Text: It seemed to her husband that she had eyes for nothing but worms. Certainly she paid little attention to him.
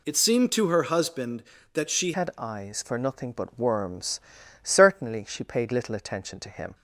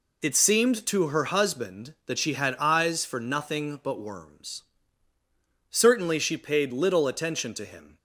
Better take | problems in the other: second | changes voice at "had"; from 2.1 s on; 4.6 s long

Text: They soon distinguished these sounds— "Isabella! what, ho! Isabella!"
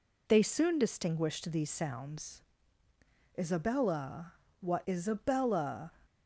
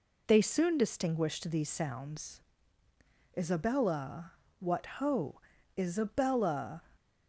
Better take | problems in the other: second | skips "ho"; at 4.8 s

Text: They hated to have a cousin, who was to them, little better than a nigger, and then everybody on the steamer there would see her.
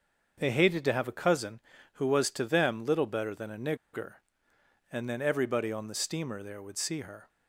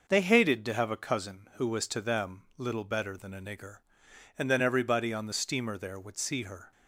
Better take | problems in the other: second | starts louder than the rest; until 1.3 s; 6.5 dB // pauses between "a" and "nigger"; slight; at 3.7 s; 0.16 s long

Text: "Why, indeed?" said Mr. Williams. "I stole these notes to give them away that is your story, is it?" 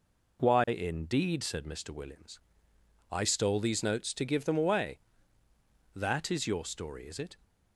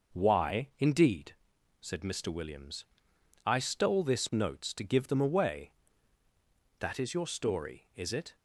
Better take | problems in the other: first | says "this" for "these"; at 4.0 s

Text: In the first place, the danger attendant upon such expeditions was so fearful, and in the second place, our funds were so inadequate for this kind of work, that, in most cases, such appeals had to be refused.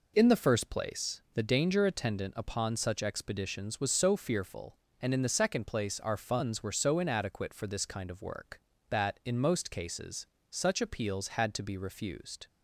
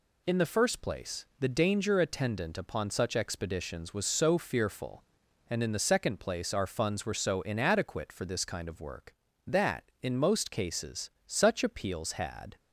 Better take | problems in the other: first | stops before "to be refused"; at 12.5 s

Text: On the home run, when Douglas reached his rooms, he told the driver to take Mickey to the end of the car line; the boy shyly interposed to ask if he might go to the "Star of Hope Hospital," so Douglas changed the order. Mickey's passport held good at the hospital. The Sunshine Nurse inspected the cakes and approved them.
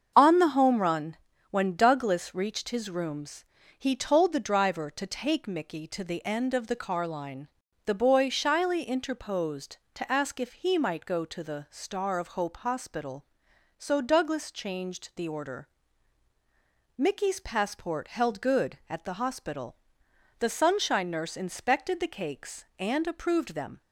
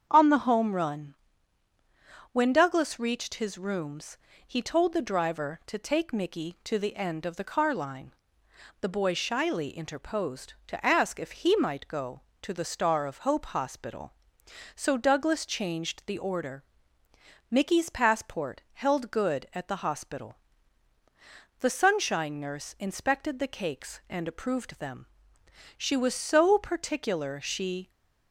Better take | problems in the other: first | starts louder than the rest; strong; until 1.1 s; 7.5 dB; strong in the first // goes on to say "She was so particular she"; strong; from 25.7 s on; 2.1 s long

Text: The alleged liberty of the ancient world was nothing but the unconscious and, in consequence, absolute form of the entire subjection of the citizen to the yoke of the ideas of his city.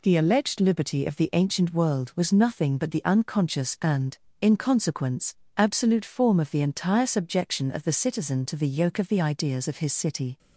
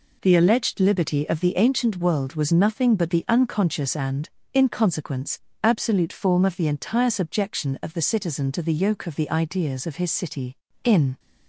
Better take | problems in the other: first | goes on to say "In"; slight; from 10.8 s on; 0.36 s long

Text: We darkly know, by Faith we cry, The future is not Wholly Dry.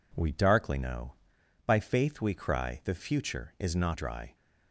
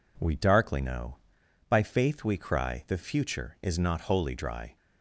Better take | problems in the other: second | skips "Wholly"; at 3.9 s

